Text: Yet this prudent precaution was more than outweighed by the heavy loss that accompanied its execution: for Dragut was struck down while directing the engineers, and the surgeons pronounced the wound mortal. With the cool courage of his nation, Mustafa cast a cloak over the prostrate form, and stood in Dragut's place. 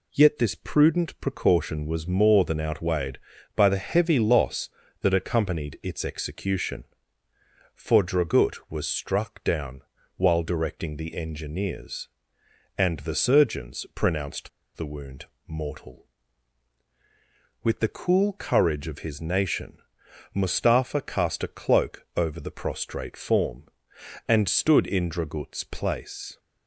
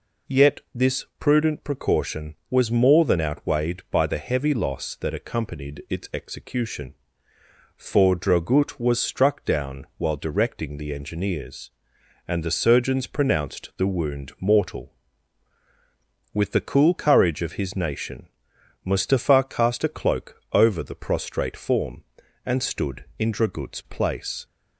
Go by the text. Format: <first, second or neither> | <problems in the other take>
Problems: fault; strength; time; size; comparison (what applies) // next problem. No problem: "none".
second | pauses between "down" and "while"; slight; at 9.8 s; 0.34 s long // pauses between "pronounced" and "the"; slight; at 14.4 s; 0.26 s long // pauses between "wound" and "mortal"; slight; at 15.2 s; 0.20 s long